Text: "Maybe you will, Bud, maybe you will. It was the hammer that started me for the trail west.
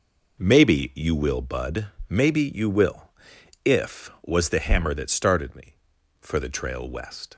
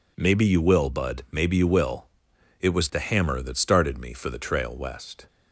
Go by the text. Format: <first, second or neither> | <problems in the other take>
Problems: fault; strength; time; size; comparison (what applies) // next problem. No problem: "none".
second | says "If" for "It"; at 3.6 s